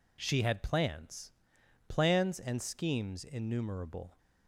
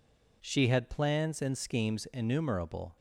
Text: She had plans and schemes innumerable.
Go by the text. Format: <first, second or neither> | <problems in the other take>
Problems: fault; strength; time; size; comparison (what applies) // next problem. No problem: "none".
second | says "plans" twice; at 1.8 s